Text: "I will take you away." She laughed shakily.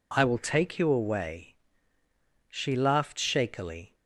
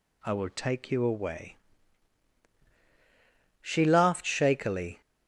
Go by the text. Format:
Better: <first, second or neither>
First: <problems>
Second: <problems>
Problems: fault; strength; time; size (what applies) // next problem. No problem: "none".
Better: neither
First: none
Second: none